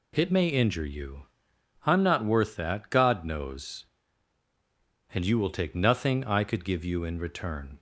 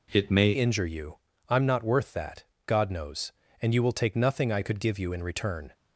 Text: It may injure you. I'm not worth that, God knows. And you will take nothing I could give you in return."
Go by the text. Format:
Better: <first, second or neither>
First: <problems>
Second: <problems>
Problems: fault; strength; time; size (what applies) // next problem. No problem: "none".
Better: first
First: none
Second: changes voice at "injure"; from 0.5 s on; 5.2 s long